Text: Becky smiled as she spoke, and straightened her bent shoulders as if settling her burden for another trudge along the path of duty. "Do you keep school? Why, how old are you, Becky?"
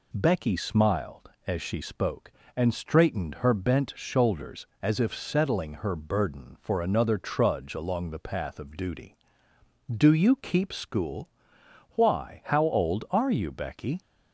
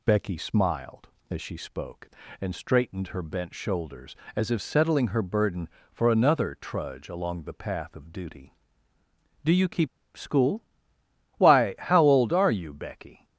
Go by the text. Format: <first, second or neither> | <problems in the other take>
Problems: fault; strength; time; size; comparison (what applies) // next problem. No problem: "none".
first | pauses between "keep" and "school"; slight; at 9.8 s; 0.29 s long